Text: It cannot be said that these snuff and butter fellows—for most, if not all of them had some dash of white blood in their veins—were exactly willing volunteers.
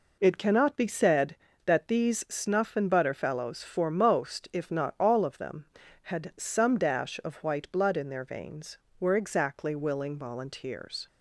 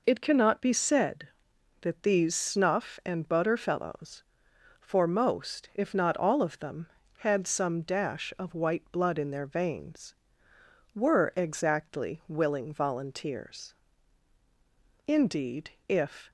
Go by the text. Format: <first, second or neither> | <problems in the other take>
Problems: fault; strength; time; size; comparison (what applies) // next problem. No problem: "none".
first | goes on to say "Indeed if"; noticeable; from 15.0 s on; 1.2 s long